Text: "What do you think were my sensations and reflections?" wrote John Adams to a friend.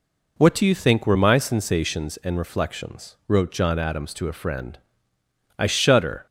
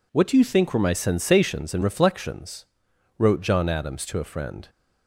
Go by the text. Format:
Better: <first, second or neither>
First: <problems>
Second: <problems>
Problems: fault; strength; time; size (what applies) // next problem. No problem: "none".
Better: second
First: goes on to say "I shudder"; noticeable; from 5.5 s on; 0.66 s long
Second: none